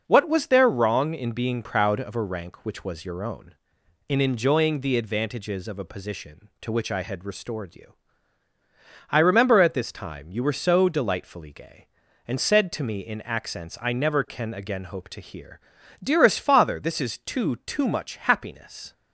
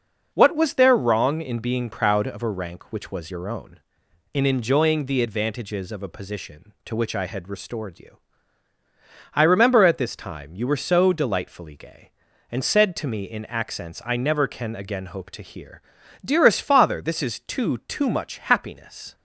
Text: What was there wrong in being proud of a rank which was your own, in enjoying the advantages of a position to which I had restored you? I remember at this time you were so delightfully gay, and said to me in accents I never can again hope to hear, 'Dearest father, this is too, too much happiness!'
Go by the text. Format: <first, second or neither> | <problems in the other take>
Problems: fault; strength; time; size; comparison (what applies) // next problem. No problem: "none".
neither | none